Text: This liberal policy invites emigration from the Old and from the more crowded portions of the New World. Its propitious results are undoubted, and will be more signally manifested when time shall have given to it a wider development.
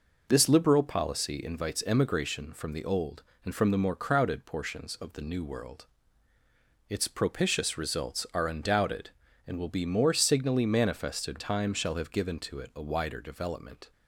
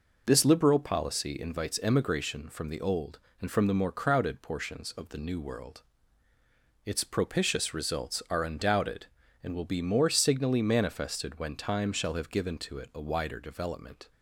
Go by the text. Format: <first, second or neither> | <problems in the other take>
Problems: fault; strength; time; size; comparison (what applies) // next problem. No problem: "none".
second | skips "when"; at 11.4 s